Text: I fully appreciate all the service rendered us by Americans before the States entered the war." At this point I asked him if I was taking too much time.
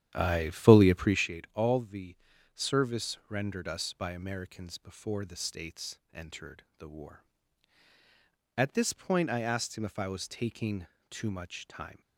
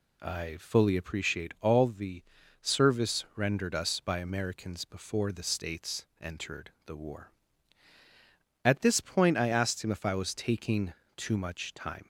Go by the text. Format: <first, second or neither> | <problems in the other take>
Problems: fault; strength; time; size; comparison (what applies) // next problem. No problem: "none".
second | starts louder than the rest; strong; until 1.3 s; 10.5 dB // pauses between "the" and "service"; at 2.1 s; 0.40 s long; also in the second // pauses between "taking" and "too"; slight; at 10.8 s; 0.24 s long; slight in the second